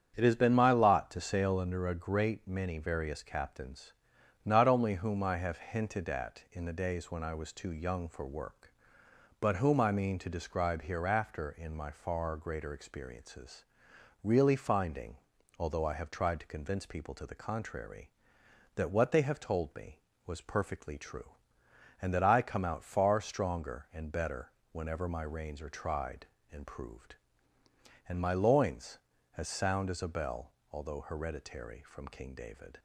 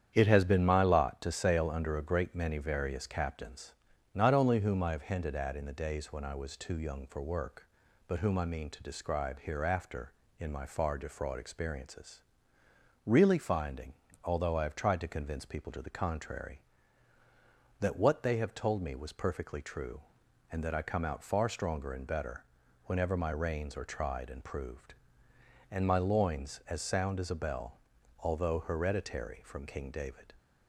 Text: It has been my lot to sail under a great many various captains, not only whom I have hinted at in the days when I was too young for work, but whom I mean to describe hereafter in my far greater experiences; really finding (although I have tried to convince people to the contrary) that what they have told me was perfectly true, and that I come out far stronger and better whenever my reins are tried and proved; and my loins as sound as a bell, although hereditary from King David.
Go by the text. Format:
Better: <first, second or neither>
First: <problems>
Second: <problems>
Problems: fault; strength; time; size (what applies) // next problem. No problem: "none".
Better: first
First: starts louder than the rest; strong; until 1.1 s; 8 dB // pauses between "better" and "whenever"; slight; at 24.5 s; 0.18 s long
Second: starts louder than the rest; strong; until 1.1 s; 9 dB // says "defraud" for "greater"; at 10.9 s // pauses between "better" and "whenever"; at 22.4 s; 0.40 s long